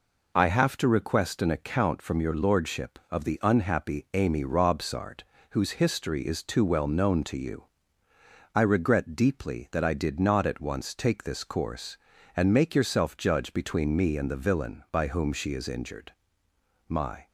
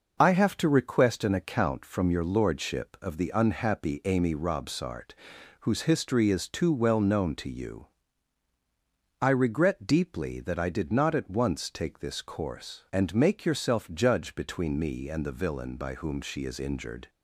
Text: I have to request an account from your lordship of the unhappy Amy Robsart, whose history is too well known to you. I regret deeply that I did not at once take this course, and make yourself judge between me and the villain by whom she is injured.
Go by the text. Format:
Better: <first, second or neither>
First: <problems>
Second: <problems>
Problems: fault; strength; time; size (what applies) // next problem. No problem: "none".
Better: second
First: goes on to say "My"; slight; from 16.8 s on; 0.42 s long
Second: none